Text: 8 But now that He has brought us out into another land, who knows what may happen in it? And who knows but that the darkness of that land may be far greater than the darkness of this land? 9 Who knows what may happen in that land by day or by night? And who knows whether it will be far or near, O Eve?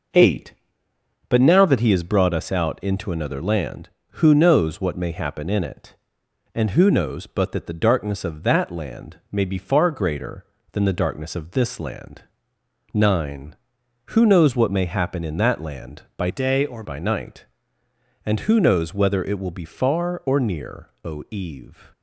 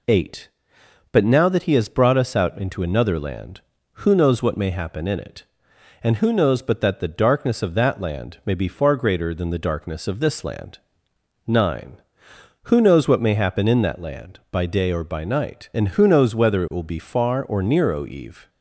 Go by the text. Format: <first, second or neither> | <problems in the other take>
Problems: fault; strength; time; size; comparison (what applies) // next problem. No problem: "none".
second | changes voice from "day" to "or"; from 16.2 to 16.8 s; 0.6 s long